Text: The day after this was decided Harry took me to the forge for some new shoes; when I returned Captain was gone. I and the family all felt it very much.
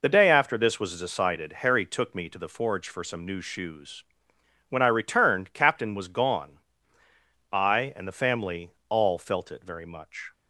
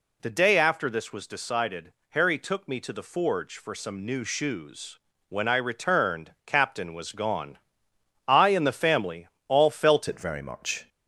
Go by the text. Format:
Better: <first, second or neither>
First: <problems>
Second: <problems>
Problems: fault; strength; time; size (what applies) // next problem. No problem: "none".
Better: first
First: pauses between "family" and "all"; slight; at 8.7 s; 0.18 s long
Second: pauses between "decided" and "Harry"; slight; at 1.9 s; 0.16 s long // pauses between "family" and "all"; slight; at 9.2 s; 0.18 s long // changes voice at "it"; from 10.0 s on; 0.8 s long